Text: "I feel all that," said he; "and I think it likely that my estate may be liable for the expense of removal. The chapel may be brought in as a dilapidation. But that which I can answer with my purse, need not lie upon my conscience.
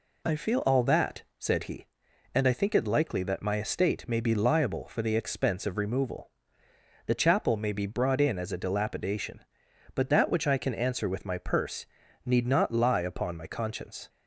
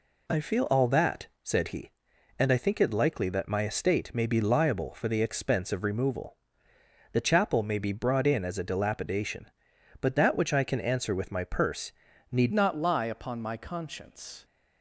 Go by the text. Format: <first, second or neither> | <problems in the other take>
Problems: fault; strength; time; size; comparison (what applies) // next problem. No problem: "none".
first | changes voice at "not"; from 12.5 s on; 1.9 s long